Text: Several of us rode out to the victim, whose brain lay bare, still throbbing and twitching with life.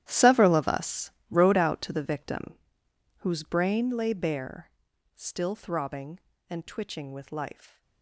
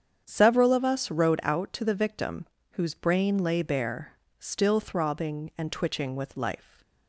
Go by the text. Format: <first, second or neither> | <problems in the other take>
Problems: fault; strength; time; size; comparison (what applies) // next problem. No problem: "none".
second | gets quieter; strong; throughout; 16.5 dB // starts louder than the rest; strong; until 1.0 s; 12 dB; strong in the second // pauses between "us" and "rode"; slight; at 1.1 s; 0.18 s long